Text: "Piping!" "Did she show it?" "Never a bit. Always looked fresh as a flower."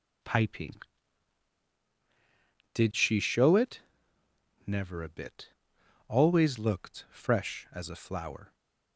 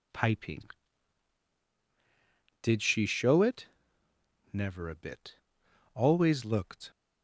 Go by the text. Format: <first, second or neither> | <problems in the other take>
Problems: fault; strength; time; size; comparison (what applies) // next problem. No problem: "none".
first | stops before "fresh as a flower"; at 6.9 s